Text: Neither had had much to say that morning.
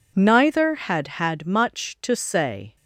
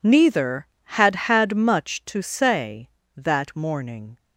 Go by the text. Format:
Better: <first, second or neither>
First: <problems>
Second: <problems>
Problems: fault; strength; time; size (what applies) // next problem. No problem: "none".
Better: second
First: stops before "that morning"; at 2.7 s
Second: none